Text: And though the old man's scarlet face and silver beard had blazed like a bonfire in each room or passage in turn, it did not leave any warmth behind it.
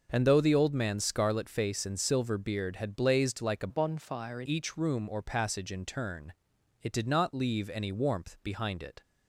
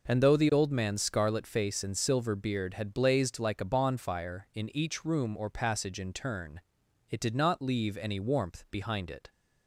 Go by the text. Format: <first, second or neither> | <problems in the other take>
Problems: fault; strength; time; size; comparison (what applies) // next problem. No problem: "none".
second | changes voice from "bonfire" to "in"; from 3.6 to 4.4 s; 0.8 s long